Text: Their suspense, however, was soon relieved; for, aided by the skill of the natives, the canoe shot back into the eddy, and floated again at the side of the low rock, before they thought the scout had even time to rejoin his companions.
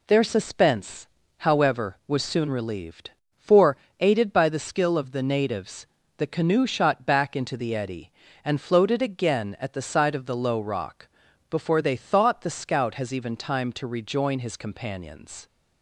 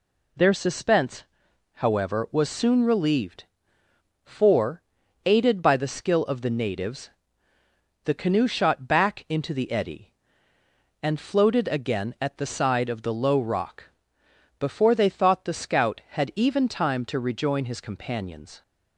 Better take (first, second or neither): second